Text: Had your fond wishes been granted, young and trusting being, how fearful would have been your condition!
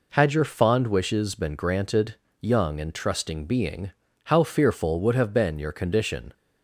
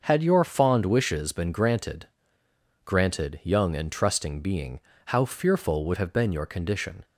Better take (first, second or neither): first